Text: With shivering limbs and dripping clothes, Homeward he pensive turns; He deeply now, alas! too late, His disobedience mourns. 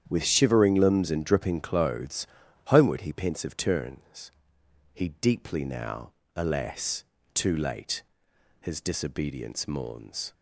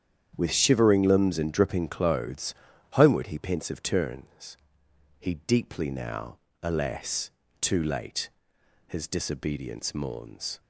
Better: neither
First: starts louder than the rest; strong; until 1.0 s; 9 dB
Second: starts louder than the rest; strong; until 1.3 s; 9 dB

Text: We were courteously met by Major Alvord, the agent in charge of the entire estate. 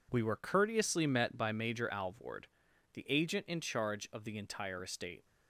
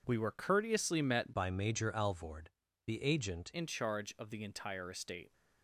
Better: first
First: none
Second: changes voice from "by" to "agent"; from 1.3 to 3.4 s; 2.1 s long

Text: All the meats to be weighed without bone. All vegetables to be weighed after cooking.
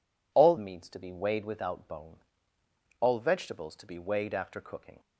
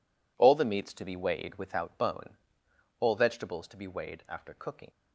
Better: second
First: skips "the"; at 0.5 s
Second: none

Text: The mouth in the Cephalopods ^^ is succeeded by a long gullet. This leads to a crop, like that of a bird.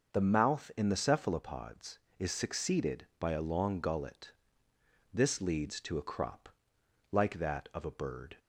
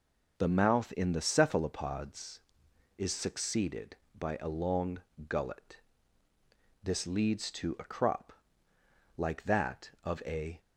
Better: first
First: none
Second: pauses between "long" and "gullet"; slight; at 4.9 s; 0.30 s long // stops before "bird"; at 10.5 s

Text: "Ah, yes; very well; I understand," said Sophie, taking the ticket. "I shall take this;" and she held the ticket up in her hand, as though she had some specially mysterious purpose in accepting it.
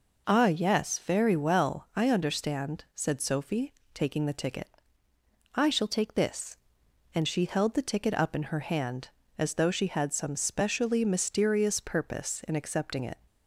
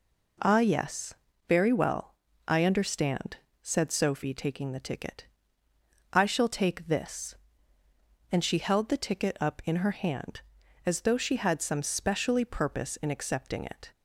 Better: first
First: none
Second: skips "mysterious"; at 12.4 s

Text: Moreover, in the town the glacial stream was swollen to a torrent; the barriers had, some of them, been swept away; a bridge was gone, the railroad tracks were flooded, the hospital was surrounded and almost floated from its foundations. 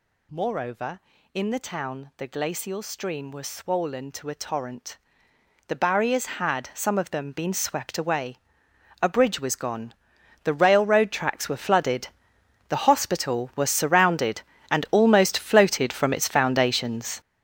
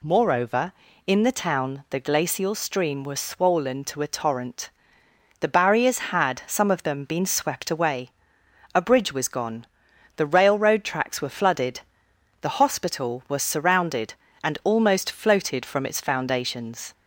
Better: second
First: gets louder; strong; throughout; 12 dB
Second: none

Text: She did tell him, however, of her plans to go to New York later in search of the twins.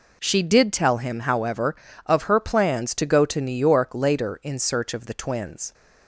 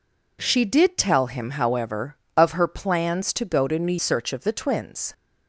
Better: first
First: none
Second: skips "York later in"; at 3.9 s

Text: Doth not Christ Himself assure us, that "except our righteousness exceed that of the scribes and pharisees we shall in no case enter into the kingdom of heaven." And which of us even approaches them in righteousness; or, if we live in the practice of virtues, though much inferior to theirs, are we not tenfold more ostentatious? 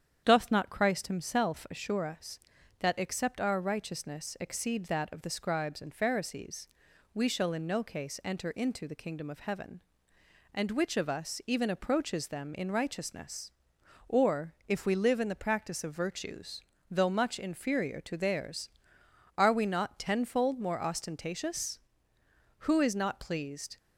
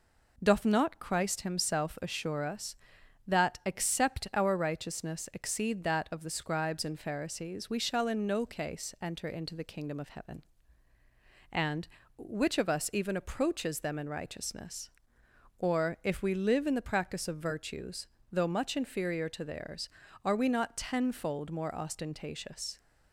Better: second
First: starts louder than the rest; strong; until 1.2 s; 8.5 dB // pauses between "pharisees" and "we"; noticeable; at 6.6 s; 0.48 s long // goes on to say "Who is not pleased"; noticeable; from 22.5 s on; 1.1 s long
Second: none

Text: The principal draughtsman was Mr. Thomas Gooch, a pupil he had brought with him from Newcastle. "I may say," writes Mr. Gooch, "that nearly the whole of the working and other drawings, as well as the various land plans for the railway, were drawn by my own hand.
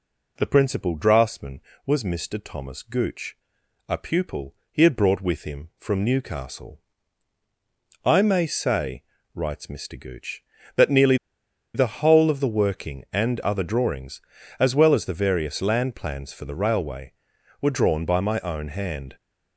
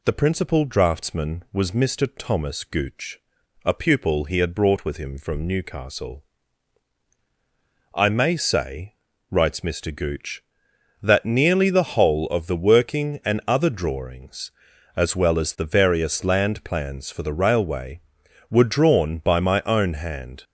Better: second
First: pauses between "pupil" and "he"; slight; at 4.5 s; 0.16 s long // pauses between "nearly" and "the"; noticeable; at 11.1 s; 0.58 s long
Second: none

